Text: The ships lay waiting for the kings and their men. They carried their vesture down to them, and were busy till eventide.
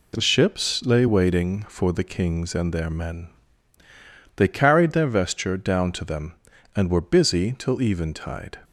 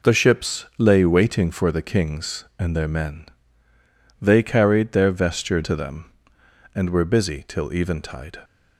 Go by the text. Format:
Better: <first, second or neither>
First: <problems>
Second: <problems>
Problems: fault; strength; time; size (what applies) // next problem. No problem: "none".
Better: first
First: none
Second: skips "down"; at 5.6 s